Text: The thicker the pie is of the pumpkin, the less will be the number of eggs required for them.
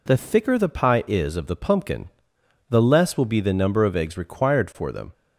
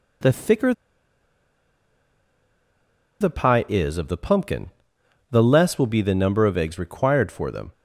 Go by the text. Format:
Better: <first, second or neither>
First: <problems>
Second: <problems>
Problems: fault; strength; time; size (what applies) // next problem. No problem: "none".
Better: first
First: none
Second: pauses between "thicker" and "the"; strong; at 0.7 s; 2.4 s long